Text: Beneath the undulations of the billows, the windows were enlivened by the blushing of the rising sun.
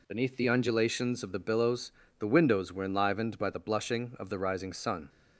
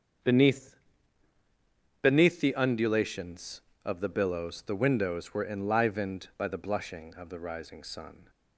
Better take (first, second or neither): first